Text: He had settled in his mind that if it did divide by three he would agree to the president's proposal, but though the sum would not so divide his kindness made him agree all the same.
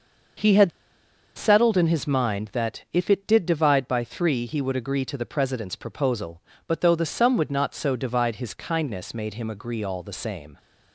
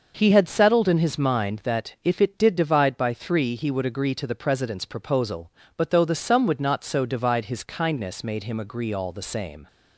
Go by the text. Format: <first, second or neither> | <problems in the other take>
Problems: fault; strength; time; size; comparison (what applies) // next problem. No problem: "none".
second | pauses between "had" and "settled"; noticeable; at 0.7 s; 0.65 s long